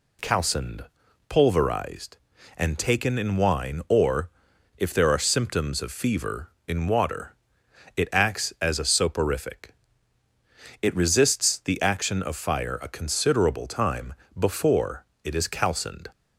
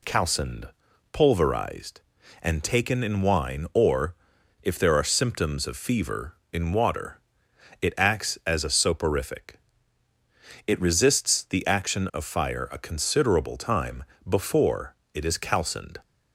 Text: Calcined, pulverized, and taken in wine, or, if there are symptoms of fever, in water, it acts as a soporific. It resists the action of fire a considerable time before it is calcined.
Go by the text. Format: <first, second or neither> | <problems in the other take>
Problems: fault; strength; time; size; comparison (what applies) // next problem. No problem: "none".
neither | pauses between "time" and "before"; slight; the same in both // pauses between "before" and "it"; slight; the same in both